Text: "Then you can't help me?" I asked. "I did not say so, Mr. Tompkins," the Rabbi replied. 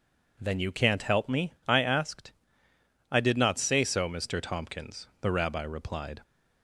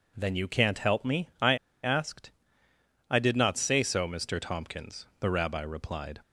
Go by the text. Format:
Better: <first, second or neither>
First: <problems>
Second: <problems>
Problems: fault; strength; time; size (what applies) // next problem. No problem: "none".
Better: first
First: none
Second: pauses between "I" and "asked"; slight; at 1.5 s; 0.27 s long